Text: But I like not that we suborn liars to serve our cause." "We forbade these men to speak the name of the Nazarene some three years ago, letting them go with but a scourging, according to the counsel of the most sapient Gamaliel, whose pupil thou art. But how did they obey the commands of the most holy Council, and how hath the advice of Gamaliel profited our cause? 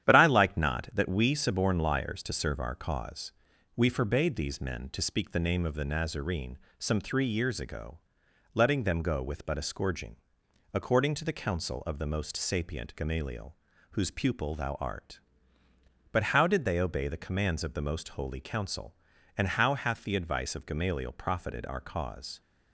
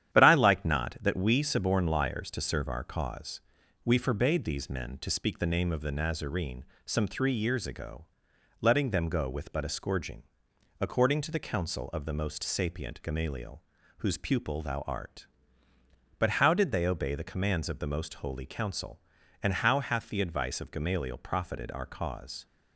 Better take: neither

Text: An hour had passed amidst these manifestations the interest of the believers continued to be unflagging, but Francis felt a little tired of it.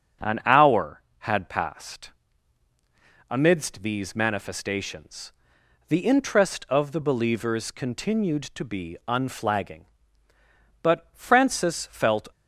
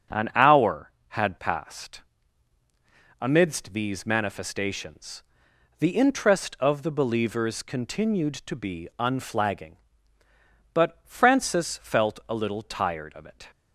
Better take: second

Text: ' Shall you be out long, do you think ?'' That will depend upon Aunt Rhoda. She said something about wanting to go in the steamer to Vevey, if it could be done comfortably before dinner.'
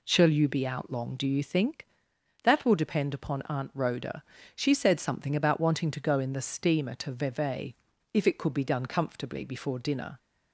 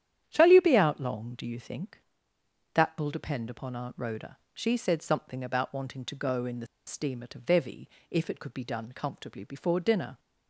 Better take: first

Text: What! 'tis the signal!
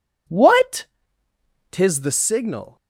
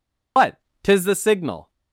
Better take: first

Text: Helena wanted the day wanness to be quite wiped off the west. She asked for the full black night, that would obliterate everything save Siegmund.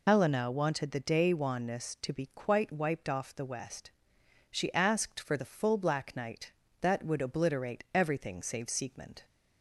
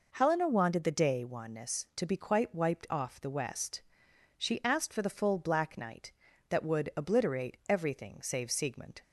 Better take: second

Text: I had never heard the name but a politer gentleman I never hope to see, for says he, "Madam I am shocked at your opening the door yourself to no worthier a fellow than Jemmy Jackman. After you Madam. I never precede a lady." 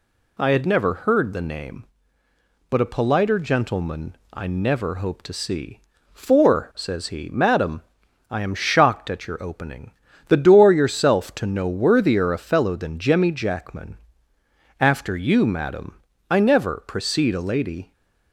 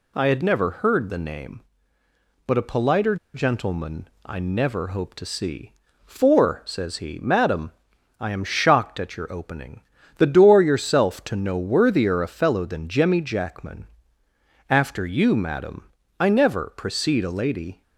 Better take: first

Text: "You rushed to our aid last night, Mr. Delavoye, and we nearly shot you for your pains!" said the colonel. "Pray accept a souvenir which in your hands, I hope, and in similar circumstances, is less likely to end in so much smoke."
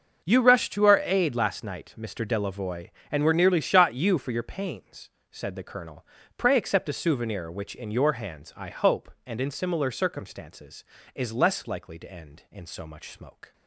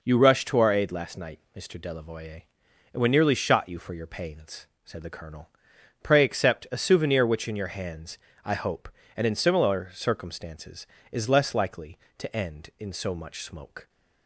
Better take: second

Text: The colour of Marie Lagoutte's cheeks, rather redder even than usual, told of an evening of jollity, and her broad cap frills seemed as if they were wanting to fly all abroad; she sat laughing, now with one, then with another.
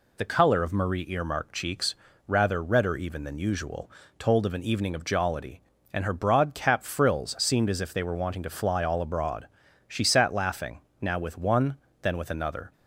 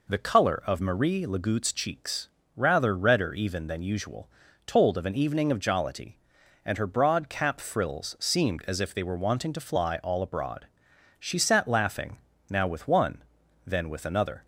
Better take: second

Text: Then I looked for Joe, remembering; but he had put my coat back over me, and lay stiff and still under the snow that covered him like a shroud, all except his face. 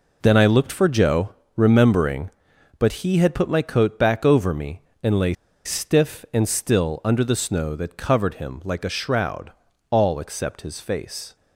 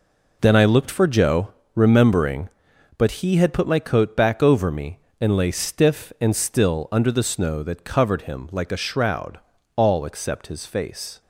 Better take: second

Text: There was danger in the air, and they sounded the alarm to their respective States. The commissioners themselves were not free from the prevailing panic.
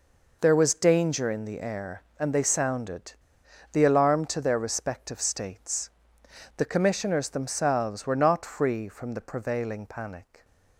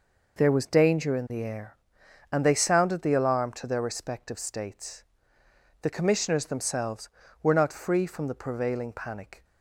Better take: second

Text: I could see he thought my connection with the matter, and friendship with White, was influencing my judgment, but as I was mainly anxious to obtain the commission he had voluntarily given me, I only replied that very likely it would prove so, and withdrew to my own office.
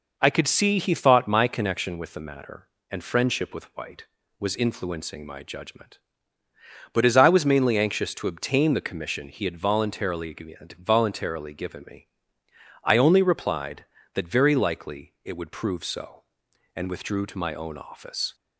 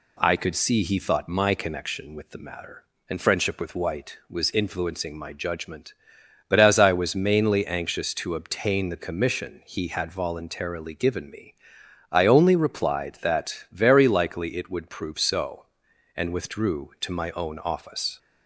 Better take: second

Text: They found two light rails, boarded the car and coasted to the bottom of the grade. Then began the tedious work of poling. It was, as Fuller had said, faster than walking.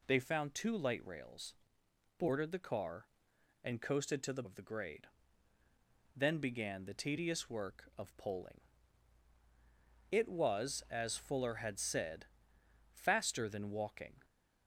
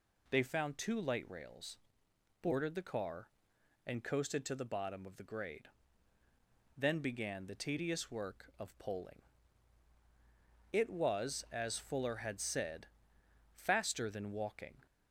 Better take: second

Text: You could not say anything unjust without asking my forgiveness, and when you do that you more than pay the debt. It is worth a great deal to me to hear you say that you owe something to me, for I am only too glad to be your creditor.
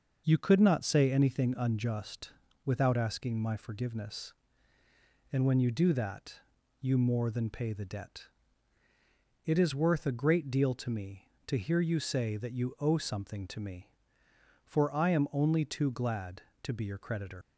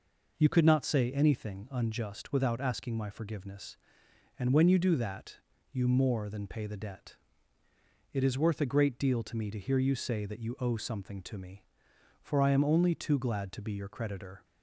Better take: second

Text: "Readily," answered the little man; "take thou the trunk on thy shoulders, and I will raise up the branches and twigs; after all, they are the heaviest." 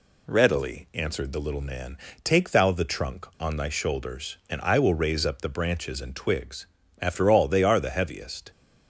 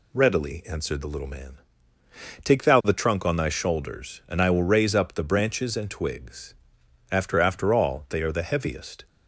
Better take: first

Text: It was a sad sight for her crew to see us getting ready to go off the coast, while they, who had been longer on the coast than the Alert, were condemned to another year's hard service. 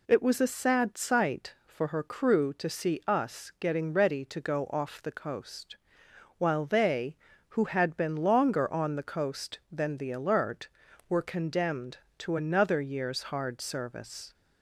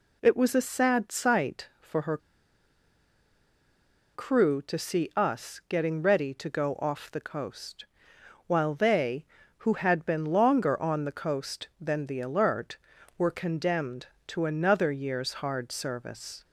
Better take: first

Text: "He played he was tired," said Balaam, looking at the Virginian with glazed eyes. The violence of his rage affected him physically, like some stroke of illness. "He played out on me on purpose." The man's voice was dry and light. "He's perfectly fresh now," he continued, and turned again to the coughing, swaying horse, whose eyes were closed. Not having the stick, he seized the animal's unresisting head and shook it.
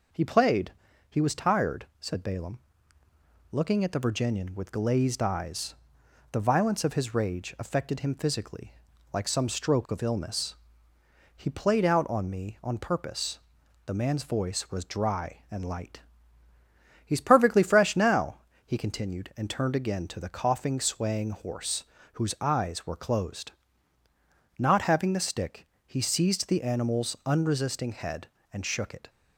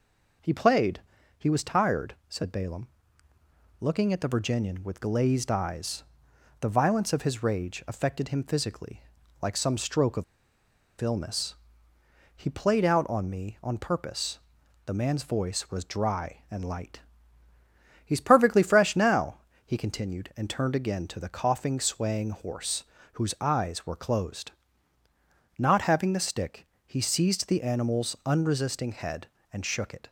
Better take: first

